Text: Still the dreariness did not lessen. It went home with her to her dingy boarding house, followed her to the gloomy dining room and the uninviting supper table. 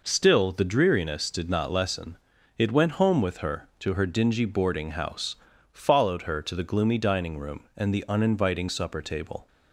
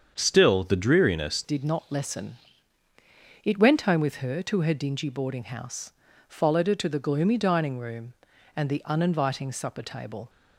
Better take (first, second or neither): first